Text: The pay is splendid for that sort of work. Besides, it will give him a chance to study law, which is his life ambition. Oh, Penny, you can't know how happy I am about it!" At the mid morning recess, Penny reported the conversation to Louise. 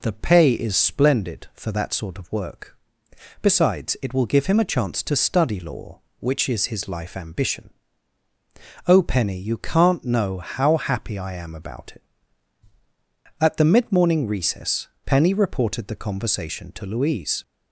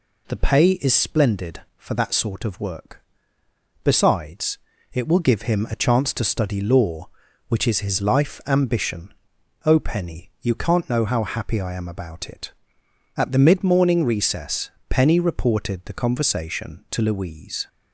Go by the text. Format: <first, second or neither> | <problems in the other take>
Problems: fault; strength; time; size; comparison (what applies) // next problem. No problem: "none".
neither | none